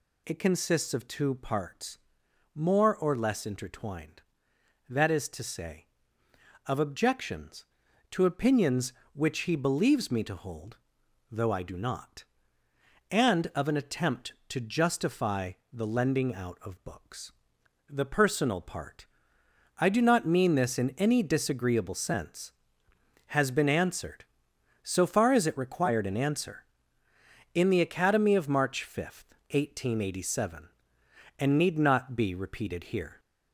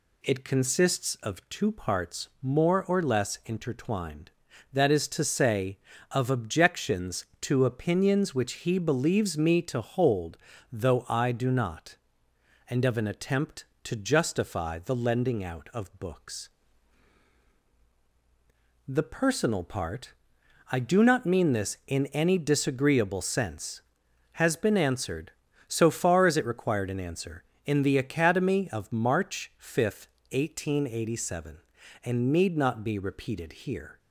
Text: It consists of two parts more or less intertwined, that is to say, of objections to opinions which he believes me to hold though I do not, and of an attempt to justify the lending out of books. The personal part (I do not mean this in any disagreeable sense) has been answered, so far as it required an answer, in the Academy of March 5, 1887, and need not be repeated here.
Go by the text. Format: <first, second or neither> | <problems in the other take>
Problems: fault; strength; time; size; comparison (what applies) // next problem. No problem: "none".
second | gets louder; slight; throughout; 2.5 dB // pauses between "parts" and "more"; noticeable; at 1.9 s; 0.58 s long; slight in the second // pauses between "hold" and "though"; noticeable; at 10.7 s; 0.56 s long; slight in the second // pauses between "justify" and "the"; slight; at 15.5 s; 0.20 s long